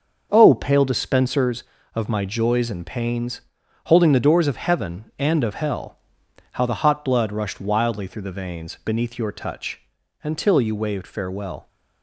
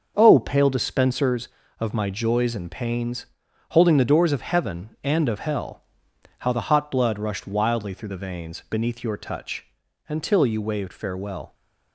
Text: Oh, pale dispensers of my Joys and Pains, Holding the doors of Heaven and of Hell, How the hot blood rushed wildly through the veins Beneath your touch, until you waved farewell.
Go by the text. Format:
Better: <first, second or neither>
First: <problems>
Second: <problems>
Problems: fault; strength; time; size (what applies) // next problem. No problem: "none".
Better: neither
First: starts louder than the rest; until 1.3 s; 6.5 dB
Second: starts louder than the rest; until 1.1 s; 6.5 dB